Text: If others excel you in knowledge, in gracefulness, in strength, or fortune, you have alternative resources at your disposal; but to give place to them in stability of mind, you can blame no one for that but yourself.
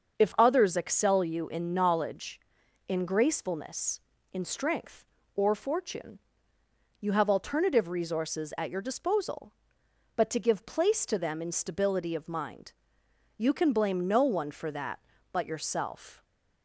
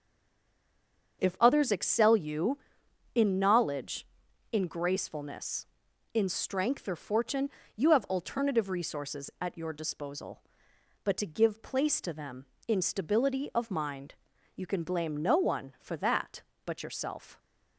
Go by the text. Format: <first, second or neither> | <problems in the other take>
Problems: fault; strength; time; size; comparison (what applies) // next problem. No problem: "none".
first | stays silent before the first word; noticeable; until 1.2 s; 1.2 s long // starts louder than the rest; until 2.2 s; 7 dB; also in the first